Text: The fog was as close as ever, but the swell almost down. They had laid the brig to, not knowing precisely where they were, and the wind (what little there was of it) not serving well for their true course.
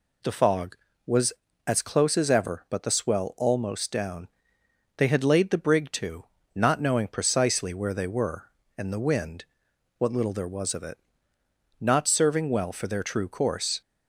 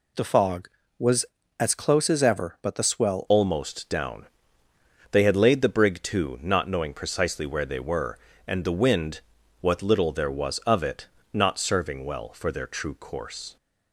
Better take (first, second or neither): first